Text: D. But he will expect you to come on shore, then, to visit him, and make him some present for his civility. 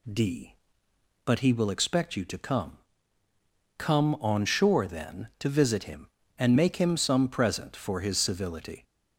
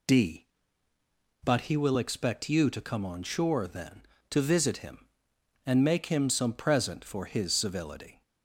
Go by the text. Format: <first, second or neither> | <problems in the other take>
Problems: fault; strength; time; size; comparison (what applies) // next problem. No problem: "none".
second | says "come" twice; at 3.7 s